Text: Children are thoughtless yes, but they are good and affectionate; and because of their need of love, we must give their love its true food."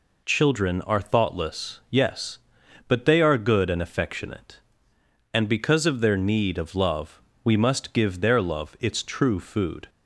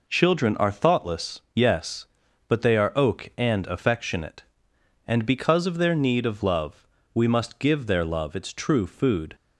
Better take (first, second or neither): first